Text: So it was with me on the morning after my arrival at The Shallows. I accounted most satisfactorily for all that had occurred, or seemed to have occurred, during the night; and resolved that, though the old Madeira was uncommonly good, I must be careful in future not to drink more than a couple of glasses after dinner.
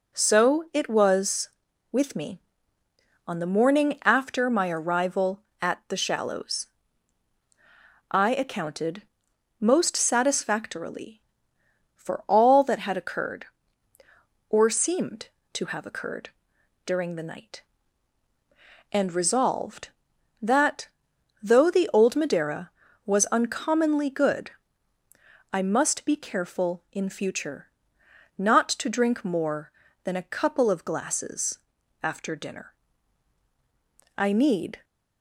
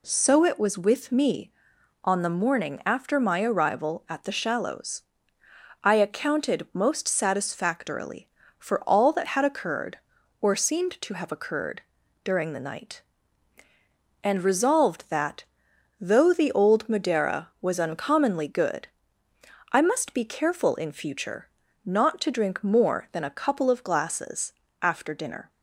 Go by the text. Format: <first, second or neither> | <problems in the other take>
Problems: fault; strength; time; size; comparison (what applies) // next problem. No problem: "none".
second | pauses between "accounted" and "most"; noticeable; at 9.0 s; 0.58 s long // pauses between "future" and "not"; noticeable; at 27.6 s; 0.72 s long; slight in the second // pauses between "glasses" and "after"; at 31.5 s; 0.42 s long; slight in the second // goes on to say "I need"; noticeable; from 34.1 s on; 0.66 s long